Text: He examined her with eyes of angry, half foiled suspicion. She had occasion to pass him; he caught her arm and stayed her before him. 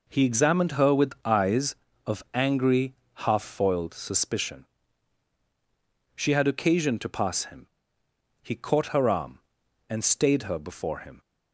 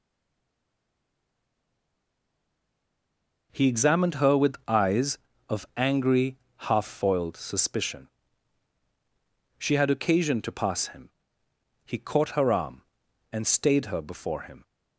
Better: first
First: none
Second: stays silent before the first word; strong; until 3.5 s; 3.5 s long

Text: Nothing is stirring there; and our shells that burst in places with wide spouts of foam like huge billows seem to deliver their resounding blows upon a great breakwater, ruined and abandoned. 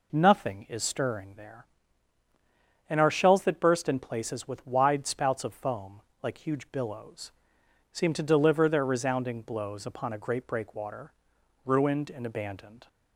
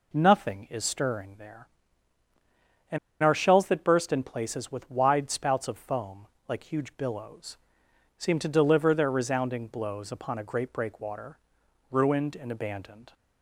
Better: first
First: pauses between "foam" and "like"; slight; at 6.0 s; 0.20 s long // pauses between "billows" and "seem"; noticeable; at 7.3 s; 0.62 s long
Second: pauses between "and" and "our"; slight; at 2.9 s; 0.24 s long // pauses between "foam" and "like"; slight; at 6.2 s; 0.20 s long // pauses between "billows" and "seem"; noticeable; at 7.5 s; 0.62 s long

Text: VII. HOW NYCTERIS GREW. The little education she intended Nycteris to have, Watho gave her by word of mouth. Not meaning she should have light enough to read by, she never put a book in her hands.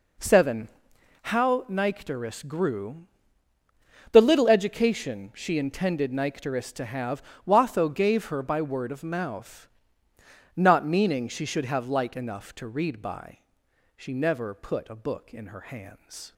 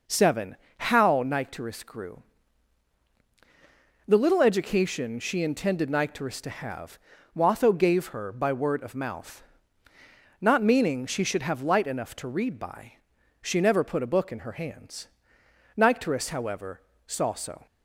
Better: first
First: none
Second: goes on to say "Nycteris however saw so"; strong; from 15.7 s on; 1.9 s long

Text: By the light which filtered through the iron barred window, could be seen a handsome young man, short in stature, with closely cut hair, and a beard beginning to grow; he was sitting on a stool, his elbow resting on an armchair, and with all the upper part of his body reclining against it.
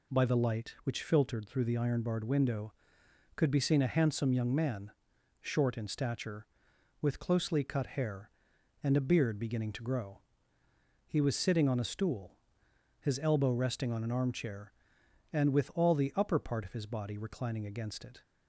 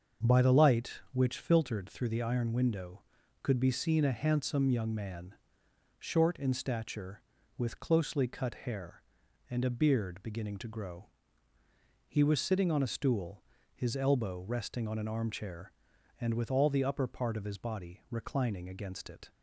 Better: first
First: none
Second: starts louder than the rest; until 1.3 s; 6.5 dB // skips "barred"; at 2.5 s

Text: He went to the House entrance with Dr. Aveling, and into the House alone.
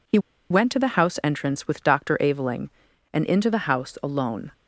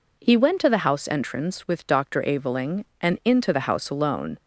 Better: second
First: pauses between "He" and "went"; slight; at 0.1 s; 0.32 s long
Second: none

